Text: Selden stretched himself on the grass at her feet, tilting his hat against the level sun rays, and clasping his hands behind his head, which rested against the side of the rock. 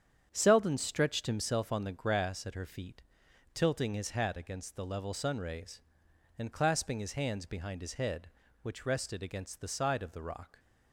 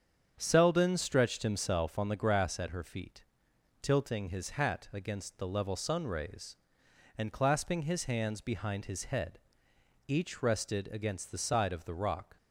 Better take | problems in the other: first | starts louder than the rest; strong; until 1.3 s; 8 dB; strong in the first // says "each" for "which"; at 10.0 s

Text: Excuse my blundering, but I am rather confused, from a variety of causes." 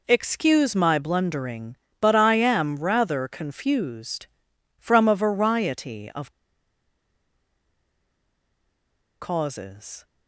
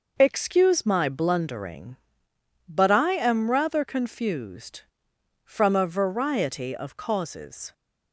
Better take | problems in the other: second | pauses between "of" and "causes"; strong; at 6.2 s; 2.9 s long

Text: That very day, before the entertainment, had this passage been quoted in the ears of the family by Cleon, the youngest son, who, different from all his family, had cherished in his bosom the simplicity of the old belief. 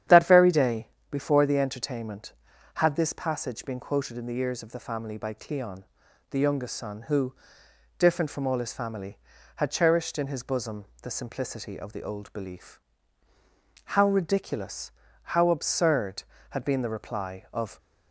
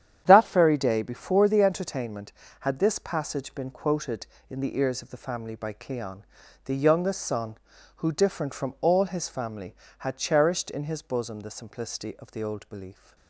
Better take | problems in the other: second | starts louder than the rest; strong; until 1.3 s; 10 dB; strong in the second // pauses between "bosom" and "the"; slight; at 10.8 s; 0.16 s long // goes on to say "How ridiculous how absurd had been the reply of"; strong; from 13.8 s on; 3.9 s long

